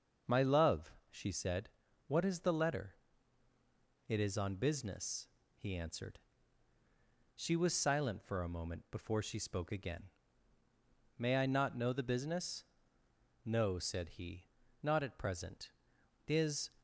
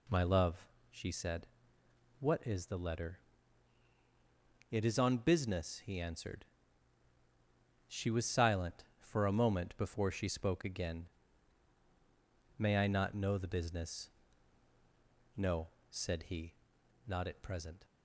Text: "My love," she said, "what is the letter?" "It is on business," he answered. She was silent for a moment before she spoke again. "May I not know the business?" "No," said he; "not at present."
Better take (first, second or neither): second